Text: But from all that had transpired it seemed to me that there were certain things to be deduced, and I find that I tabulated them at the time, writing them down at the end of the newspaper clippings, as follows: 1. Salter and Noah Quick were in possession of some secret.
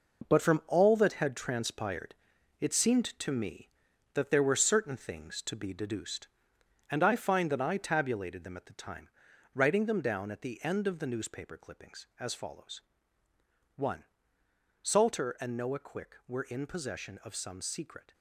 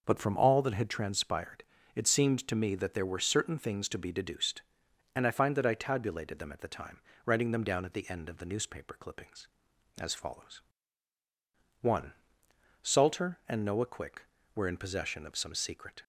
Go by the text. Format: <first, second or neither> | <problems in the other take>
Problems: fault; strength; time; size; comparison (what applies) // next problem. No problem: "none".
second | gets quieter; strong; throughout; 9 dB // pauses between "transpired" and "it"; noticeable; at 2.1 s; 0.46 s long; slight in the second